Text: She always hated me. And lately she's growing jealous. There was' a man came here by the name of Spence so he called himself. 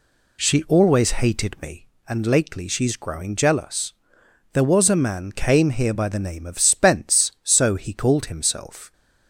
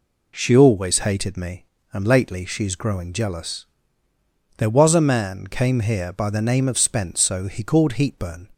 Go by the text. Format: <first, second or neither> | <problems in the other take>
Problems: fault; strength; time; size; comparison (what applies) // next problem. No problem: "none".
first | says "heatburn" for "himself"; at 7.9 s